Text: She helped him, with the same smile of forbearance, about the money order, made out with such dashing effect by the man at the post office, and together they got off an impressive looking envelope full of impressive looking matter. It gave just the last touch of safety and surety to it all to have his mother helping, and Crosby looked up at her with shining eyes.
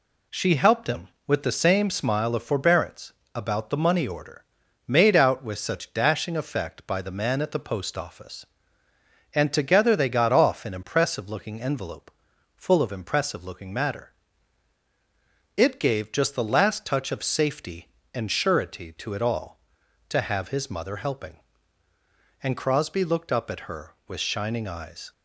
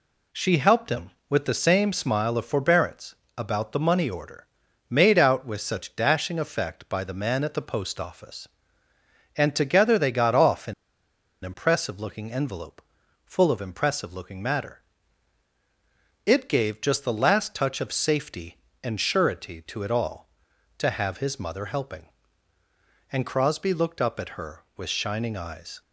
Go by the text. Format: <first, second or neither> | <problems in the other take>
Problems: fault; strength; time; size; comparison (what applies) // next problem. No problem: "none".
first | pauses between "an" and "impressive"; noticeable; at 10.7 s; 0.71 s long // pauses between "envelope" and "full"; at 12.8 s; 0.44 s long; also in the first